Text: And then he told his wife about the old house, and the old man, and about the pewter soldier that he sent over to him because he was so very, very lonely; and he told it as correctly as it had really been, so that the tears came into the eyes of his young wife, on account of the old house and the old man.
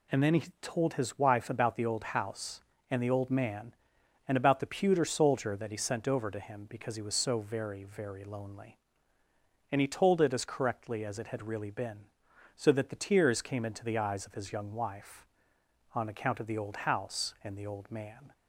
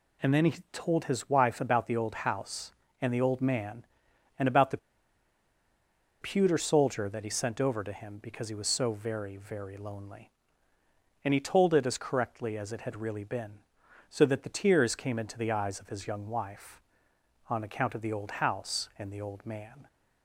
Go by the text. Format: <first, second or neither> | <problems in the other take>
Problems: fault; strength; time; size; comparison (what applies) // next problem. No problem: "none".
first | pauses between "he" and "told"; slight; at 0.5 s; 0.18 s long; slight in the first // pauses between "the" and "pewter"; strong; at 4.7 s; 1.4 s long